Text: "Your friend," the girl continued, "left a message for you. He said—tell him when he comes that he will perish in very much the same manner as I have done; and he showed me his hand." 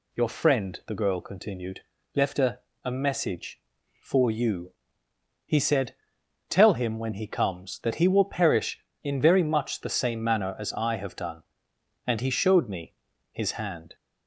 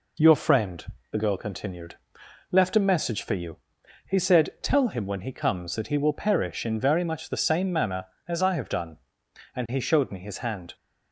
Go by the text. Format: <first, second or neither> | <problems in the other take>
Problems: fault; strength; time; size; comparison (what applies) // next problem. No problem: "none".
second | says "a" twice; at 2.8 s // pauses between "me" and "his"; at 12.9 s; 0.38 s long